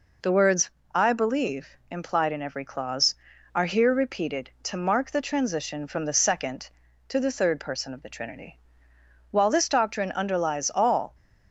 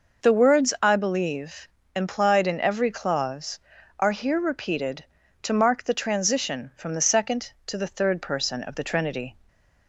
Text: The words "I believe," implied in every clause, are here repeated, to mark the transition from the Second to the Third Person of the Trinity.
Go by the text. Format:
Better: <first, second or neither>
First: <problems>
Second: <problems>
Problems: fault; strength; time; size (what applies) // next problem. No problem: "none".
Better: second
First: pauses between "words" and "I"; slight; at 0.6 s; 0.26 s long // goes on to say "While this doctrine underlies all"; strong; from 9.3 s on; 1.8 s long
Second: none